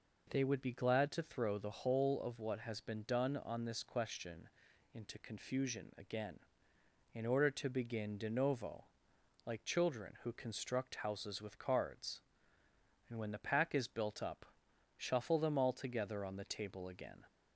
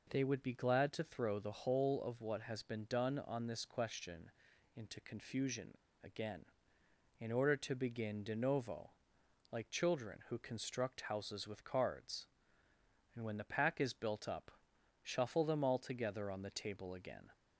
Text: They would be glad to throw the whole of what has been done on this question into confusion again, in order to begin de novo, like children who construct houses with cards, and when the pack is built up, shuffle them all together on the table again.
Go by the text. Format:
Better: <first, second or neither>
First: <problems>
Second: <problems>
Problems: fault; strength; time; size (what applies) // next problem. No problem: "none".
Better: first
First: pauses between "question" and "into"; at 4.4 s; 0.44 s long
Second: pauses between "question" and "into"; at 4.3 s; 0.44 s long // pauses between "confusion" and "again"; slight; at 5.7 s; 0.27 s long